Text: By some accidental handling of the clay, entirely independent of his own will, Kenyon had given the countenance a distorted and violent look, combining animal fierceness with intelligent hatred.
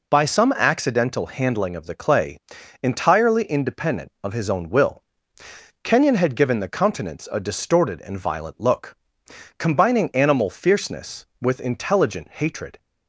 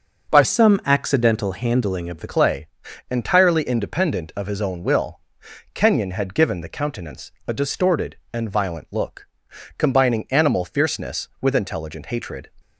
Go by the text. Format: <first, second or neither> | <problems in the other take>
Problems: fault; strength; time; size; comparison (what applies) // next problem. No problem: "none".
first | starts louder than the rest; noticeable; until 1.3 s; 6 dB // changes voice from "some" to "the"; from 0.4 to 2.2 s; 1.8 s long // pauses between "countenance" and "a"; slight; at 7.3 s; 0.16 s long